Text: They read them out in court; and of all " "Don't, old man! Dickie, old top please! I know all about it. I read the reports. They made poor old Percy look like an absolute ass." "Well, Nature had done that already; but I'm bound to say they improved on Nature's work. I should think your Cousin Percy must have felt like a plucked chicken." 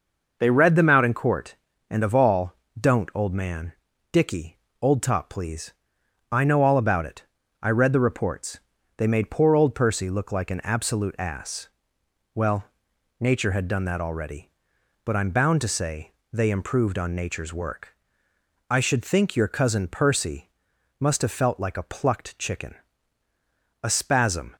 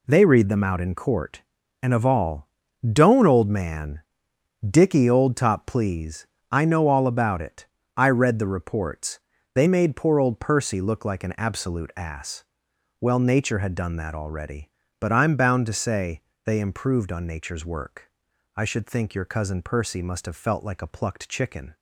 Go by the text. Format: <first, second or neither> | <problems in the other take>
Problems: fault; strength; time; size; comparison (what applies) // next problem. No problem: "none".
second | pauses between "say" and "they"; slight; at 16.1 s; 0.20 s long; slight in the second // pauses between "Percy" and "must"; noticeable; at 20.4 s; 0.50 s long // goes on to say "A spasm"; noticeable; from 23.8 s on; 0.72 s long